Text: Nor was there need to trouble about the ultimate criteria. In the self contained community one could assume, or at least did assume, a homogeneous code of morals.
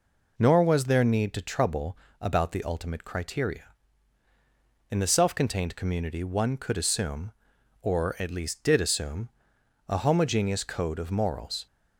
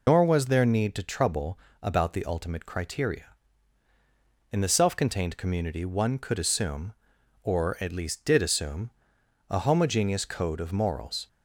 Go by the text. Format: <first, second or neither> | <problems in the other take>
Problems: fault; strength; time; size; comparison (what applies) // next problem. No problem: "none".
first | loses the start of "Nor"; at 0.0 s; 80 ms // pauses between "trouble" and "about"; slight; at 1.5 s; 0.24 s long; slight in the first